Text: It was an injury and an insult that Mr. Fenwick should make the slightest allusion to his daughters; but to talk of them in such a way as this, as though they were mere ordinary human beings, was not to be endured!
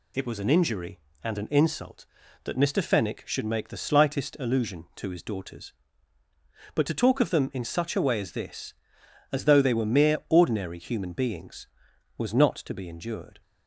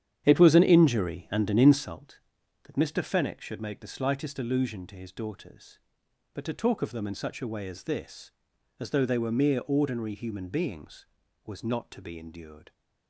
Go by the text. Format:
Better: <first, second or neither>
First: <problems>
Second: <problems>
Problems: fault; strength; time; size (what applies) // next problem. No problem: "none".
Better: first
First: none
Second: starts louder than the rest; strong; until 2.0 s; 9.5 dB